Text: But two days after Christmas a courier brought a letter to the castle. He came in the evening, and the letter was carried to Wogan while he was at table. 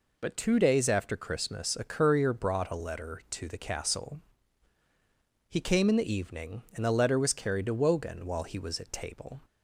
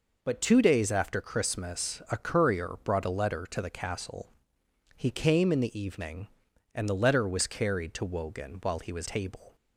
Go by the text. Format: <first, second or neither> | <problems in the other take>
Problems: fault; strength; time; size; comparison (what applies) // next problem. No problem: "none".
first | skips "at"; at 9.0 s